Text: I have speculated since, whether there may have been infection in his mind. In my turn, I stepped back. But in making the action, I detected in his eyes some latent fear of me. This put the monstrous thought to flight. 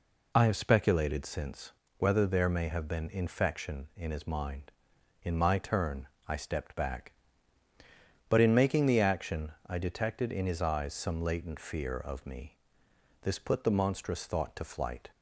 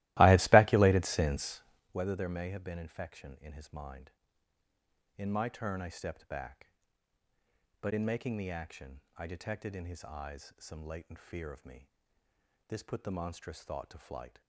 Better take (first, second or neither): first